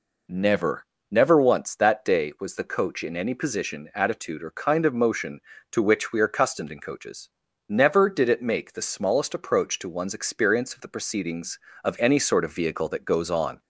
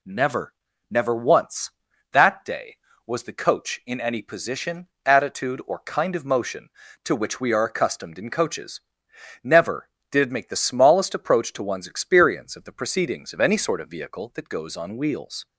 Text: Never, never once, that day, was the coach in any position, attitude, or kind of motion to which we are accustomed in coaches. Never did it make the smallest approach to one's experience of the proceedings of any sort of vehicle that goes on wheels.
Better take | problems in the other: second | stops before "wheels"; at 13.6 s

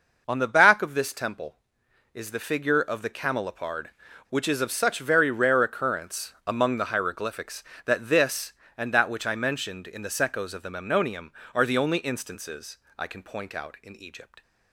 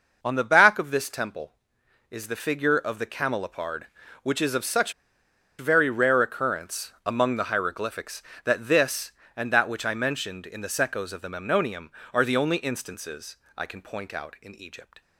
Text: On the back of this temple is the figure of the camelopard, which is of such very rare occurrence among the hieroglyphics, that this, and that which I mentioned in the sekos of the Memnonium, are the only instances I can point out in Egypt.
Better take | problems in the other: first | pauses between "such" and "very"; noticeable; at 4.9 s; 0.65 s long // pauses between "instances" and "I"; slight; at 13.3 s; 0.22 s long; slight in the first

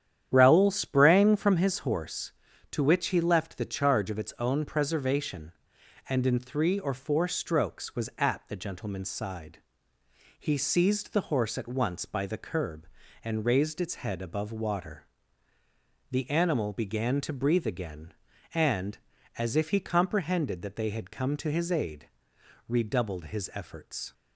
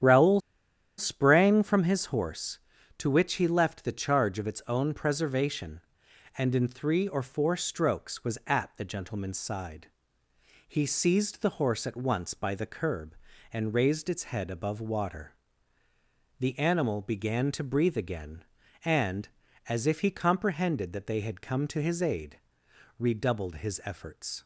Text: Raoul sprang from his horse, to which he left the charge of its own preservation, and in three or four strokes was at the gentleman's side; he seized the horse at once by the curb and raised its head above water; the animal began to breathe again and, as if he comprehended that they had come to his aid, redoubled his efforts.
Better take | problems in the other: first | starts louder than the rest; strong; until 1.6 s; 9.5 dB; strong in the first // pauses between "Raoul" and "sprang"; noticeable; at 0.3 s; 0.57 s long

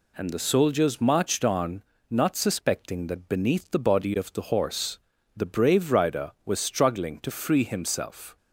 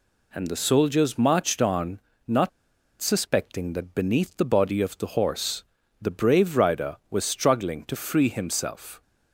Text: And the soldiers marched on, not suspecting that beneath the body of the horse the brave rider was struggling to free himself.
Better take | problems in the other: first | pauses between "not" and "suspecting"; noticeable; at 2.5 s; 0.51 s long // pauses between "horse" and "the"; slight; at 5.6 s; 0.36 s long; slight in the first

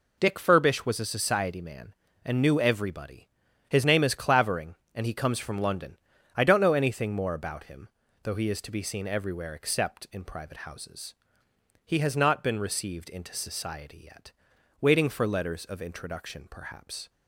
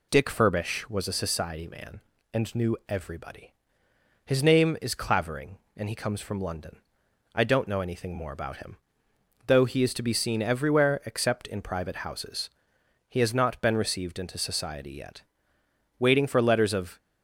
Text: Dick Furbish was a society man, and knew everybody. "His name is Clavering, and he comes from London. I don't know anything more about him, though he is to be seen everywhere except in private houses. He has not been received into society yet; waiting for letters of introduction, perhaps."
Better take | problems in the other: first | stops before "introduction perhaps"; at 16.9 s

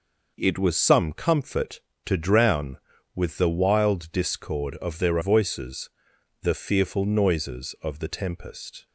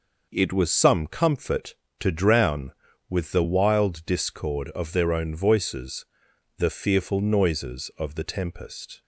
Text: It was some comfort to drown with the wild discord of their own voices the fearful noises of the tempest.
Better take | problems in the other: second | skips "own"; at 5.2 s // pauses between "voices" and "the"; noticeable; at 5.8 s; 0.54 s long; noticeable in the second

